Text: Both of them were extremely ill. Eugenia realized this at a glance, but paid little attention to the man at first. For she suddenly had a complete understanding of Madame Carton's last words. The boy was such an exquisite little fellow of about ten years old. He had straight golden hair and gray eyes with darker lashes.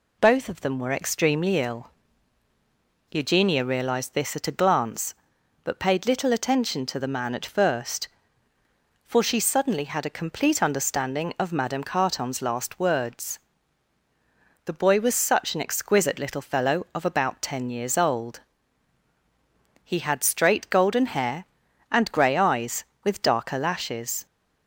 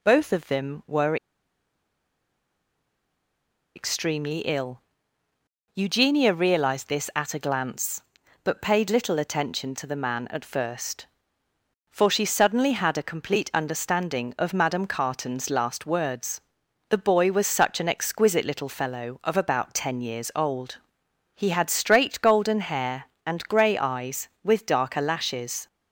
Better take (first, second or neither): first